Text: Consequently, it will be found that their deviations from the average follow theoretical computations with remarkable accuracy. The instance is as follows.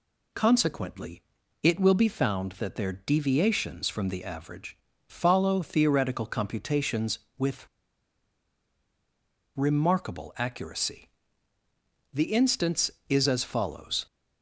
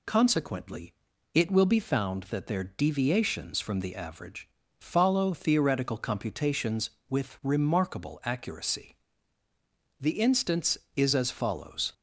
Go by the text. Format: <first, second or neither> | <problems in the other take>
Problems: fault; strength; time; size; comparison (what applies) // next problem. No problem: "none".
second | pauses between "average" and "follow"; slight; at 4.7 s; 0.32 s long; slight in the second // pauses between "with" and "remarkable"; strong; at 7.6 s; 1.9 s long